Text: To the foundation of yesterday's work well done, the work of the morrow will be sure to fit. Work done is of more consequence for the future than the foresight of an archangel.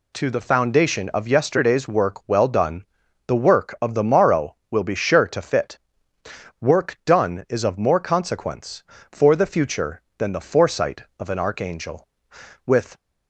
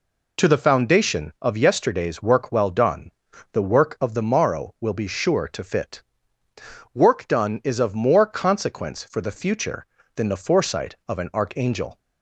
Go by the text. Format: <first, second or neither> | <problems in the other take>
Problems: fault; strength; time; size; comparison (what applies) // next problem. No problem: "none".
second | goes on to say "With"; slight; from 12.6 s on; 0.32 s long